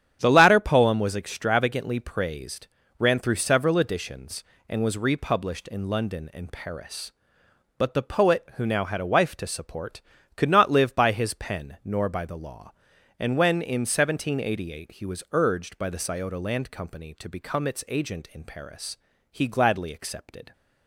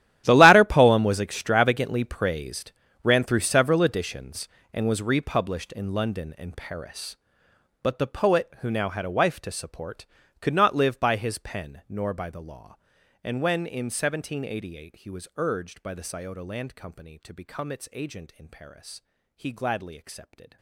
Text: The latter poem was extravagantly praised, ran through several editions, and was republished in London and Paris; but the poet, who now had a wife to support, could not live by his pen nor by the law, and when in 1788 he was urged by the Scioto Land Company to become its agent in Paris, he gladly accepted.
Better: first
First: starts louder than the rest; strong; until 1.2 s; 9.5 dB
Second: gets quieter; strong; throughout; 19 dB // starts louder than the rest; strong; until 1.2 s; 12 dB

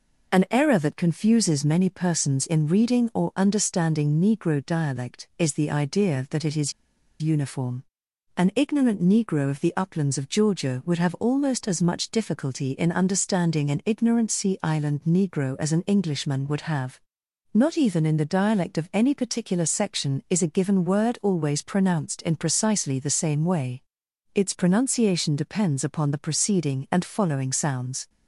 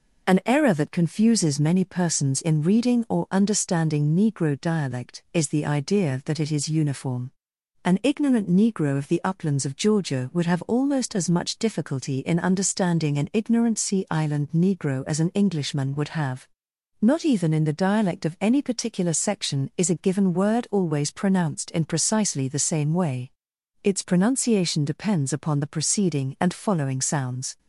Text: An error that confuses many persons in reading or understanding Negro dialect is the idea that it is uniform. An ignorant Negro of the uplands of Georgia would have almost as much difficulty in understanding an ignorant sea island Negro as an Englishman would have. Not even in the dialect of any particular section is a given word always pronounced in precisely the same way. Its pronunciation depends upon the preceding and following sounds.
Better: second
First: pauses between "is" and "uniform"; noticeable; at 6.7 s; 0.48 s long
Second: none

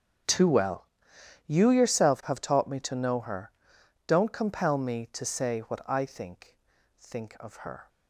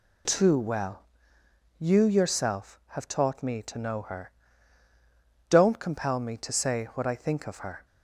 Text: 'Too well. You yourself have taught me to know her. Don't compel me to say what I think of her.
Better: second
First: starts louder than the rest; strong; until 1.8 s; 7.5 dB // says "think" twice; at 6.9 s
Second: none

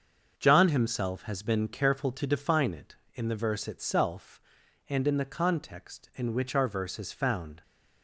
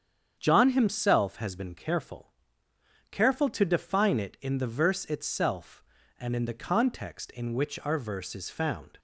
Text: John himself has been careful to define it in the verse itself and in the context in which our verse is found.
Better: first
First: starts louder than the rest; until 1.4 s; 6.5 dB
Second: starts louder than the rest; strong; until 1.3 s; 8 dB // says "careful" twice; at 3.1 s

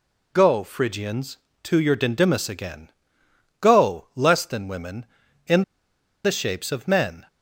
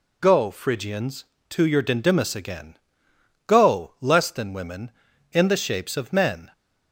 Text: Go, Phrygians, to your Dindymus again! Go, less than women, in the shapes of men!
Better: second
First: pauses between "in" and "the"; noticeable; at 5.6 s; 0.61 s long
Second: none

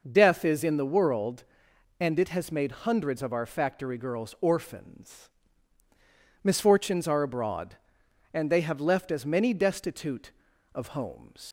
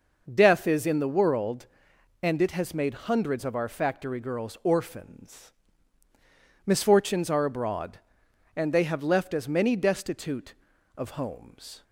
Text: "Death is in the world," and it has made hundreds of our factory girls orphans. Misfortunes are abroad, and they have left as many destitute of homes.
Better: second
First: leaves "homes" unfinished; at 11.4 s; 95 ms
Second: none

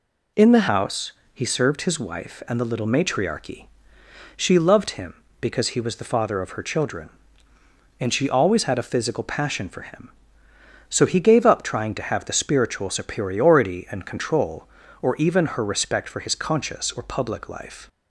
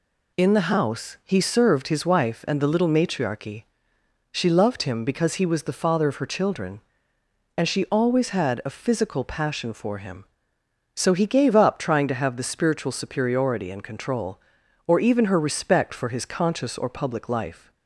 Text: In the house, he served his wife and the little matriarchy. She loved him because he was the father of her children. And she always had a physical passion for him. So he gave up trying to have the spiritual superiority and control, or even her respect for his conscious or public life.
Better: second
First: changes voice at "house"; from 0.6 s on; 17.2 s long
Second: none

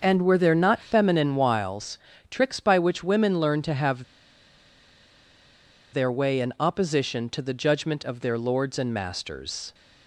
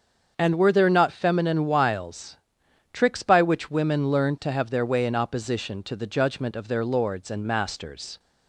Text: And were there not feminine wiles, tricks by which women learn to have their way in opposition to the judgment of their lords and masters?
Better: second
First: starts louder than the rest; noticeable; until 1.0 s; 6 dB // pauses between "have" and "their"; strong; at 4.0 s; 1.8 s long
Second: starts louder than the rest; until 1.3 s; 7 dB

